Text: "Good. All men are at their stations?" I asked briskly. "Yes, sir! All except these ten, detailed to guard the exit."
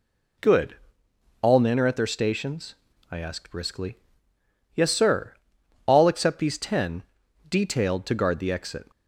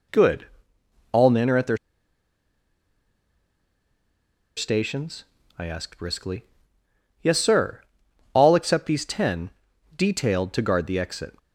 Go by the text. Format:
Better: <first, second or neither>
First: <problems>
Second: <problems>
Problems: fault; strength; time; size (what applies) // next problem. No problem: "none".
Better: first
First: none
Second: pauses between "their" and "stations"; strong; at 1.7 s; 2.8 s long